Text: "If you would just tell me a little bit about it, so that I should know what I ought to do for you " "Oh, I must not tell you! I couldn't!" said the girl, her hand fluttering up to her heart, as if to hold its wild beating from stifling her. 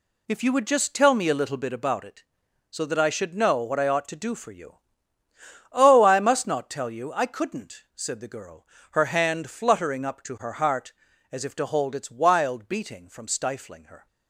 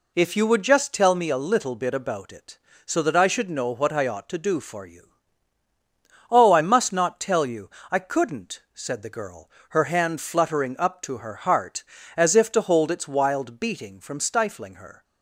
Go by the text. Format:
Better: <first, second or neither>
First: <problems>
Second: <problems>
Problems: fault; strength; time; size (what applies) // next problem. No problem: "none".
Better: neither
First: none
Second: none